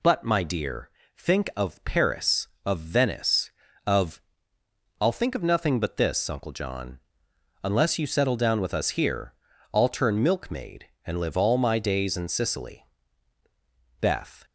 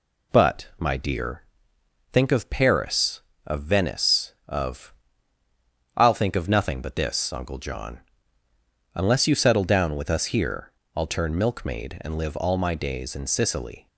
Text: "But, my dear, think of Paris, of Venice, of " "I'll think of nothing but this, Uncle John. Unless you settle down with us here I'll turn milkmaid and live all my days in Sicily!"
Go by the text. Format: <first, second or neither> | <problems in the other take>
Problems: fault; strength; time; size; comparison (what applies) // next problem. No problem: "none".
second | pauses between "here" and "I'll"; at 9.3 s; 0.40 s long; slight in the second // goes on to say "Beth"; slight; from 14.0 s on; 0.44 s long